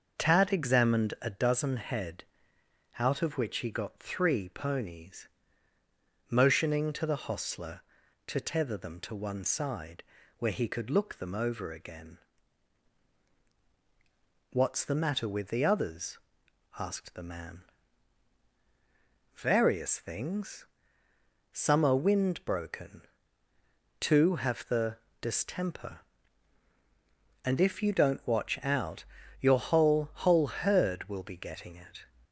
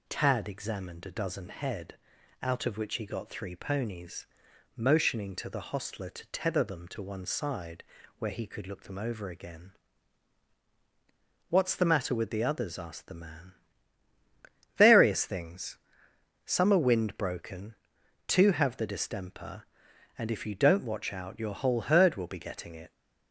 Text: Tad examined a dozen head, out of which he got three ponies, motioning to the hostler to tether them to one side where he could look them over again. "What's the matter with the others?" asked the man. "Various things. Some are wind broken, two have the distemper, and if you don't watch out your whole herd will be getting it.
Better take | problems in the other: second | starts louder than the rest; until 1.2 s; 6 dB // pauses between "side" and "where"; slight; at 10.0 s; 0.36 s long; slight in the second // pauses between "the" and "distemper"; slight; at 24.9 s; 0.24 s long // pauses between "out" and "your"; slight; at 29.0 s; 0.34 s long // says "whole" twice; at 30.1 s

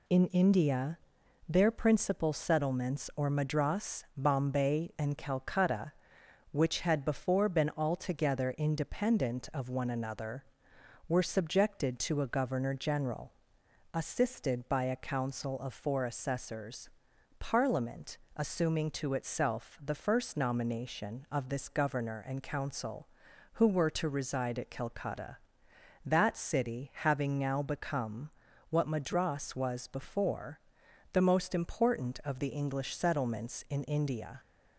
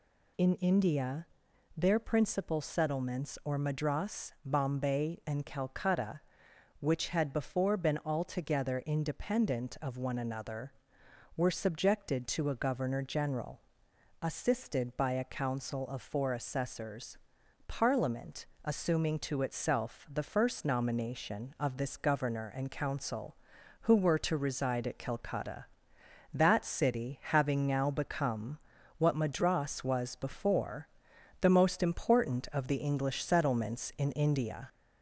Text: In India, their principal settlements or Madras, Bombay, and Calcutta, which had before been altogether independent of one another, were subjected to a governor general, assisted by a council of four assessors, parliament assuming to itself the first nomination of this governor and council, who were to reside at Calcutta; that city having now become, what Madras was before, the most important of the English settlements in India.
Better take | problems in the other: first | gets louder; slight; throughout; 2 dB // pauses between "parliament" and "assuming"; slight; at 18.4 s; 0.18 s long; slight in the first

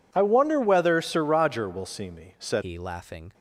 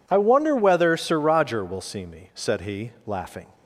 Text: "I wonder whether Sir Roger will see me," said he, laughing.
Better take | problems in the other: second | changes voice at "he"; from 2.6 s on; 0.7 s long

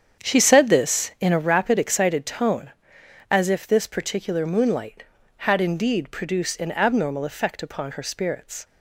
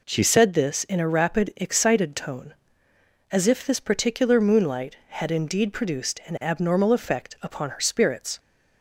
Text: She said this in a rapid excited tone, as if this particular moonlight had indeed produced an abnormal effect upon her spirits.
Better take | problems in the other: second | starts louder than the rest; strong; until 1.5 s; 8 dB

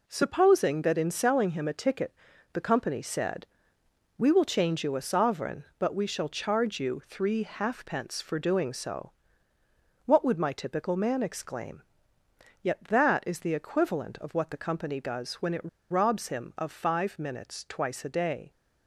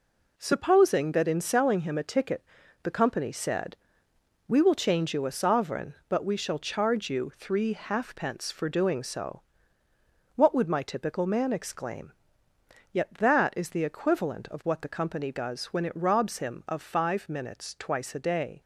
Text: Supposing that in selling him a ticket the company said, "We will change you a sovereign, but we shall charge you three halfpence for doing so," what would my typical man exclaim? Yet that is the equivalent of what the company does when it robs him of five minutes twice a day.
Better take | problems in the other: second | pauses between "ticket" and "the"; at 2.1 s; 0.38 s long; also in the second // pauses between "it" and "robs"; slight; at 15.6 s; 0.21 s long

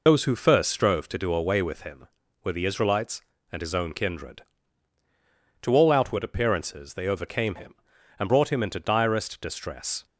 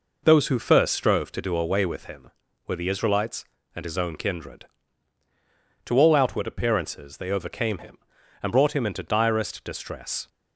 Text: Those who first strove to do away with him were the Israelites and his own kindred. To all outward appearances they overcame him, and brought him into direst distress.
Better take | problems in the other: second | loses the start of "Those"; at 0.0 s; 50 ms

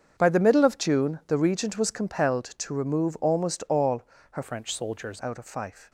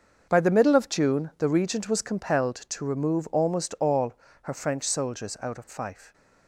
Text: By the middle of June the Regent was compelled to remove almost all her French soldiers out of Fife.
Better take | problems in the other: second | starts louder than the rest; until 1.1 s; 6.5 dB; noticeable in the second // pauses between "all" and "her"; slight; at 4.0 s; 0.30 s long; slight in the second // changes voice from "French" to "soldiers"; from 4.4 to 5.2 s; 0.8 s long

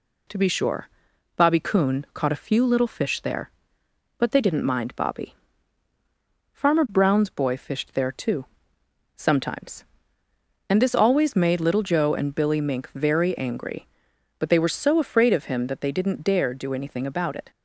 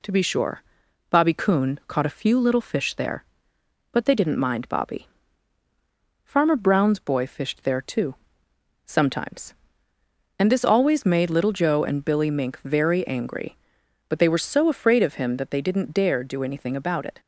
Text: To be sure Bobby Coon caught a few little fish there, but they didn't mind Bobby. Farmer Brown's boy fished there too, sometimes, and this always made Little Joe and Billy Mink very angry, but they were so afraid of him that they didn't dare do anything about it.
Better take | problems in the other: neither | pauses between "sure" and "Bobby"; noticeable; the same in both

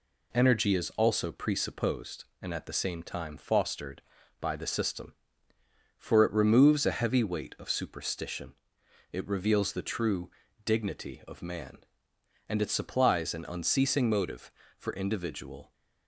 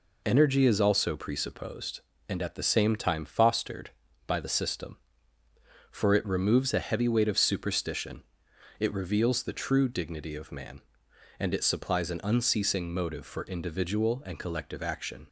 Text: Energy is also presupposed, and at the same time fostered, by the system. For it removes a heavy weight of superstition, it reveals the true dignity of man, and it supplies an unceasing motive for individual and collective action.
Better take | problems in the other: second | pauses between "true" and "dignity"; slight; at 10.3 s; 0.34 s long // stops before "and collective action"; at 15.7 s

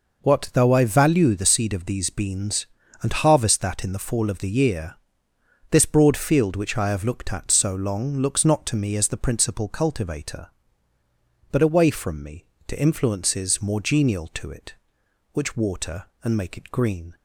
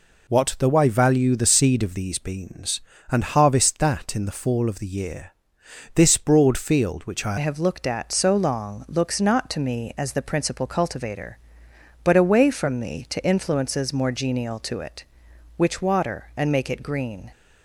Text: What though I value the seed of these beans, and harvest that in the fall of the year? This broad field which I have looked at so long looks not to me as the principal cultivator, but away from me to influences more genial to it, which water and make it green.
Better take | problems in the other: first | changes voice at "have"; from 7.3 s on; 10.0 s long

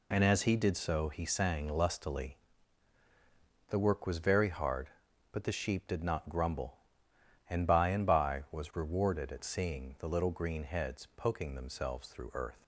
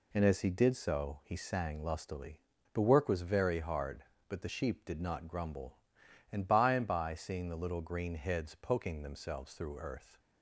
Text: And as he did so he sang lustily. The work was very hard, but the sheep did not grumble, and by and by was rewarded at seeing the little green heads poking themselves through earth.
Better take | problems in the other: first | skips "was rewarded at"; at 7.1 s

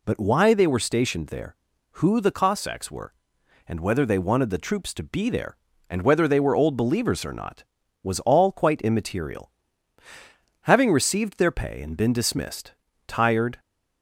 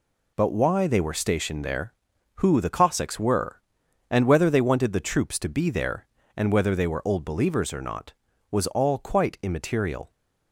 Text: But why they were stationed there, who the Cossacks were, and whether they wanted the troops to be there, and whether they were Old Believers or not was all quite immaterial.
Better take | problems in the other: second | goes on to say "Having received their pay and been dismissed tired"; strong; from 10.6 s on; 2.9 s long

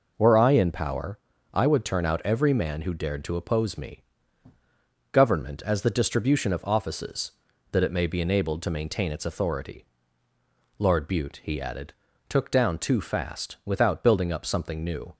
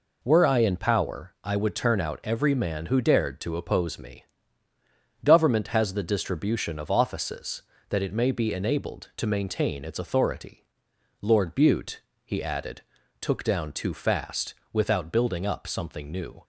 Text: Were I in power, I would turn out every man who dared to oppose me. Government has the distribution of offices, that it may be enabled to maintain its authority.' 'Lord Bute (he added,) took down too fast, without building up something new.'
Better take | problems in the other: second | says "as" for "has"; at 5.6 s

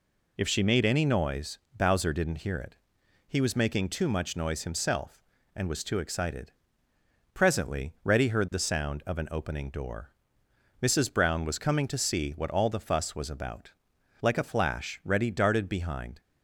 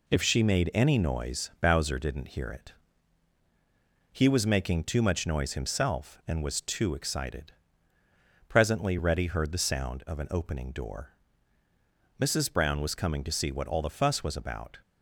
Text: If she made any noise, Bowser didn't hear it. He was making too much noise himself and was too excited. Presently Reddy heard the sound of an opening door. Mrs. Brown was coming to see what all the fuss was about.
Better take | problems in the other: second | goes on to say "Like a flash Reddy darted behind"; strong; from 14.2 s on; 2.0 s long

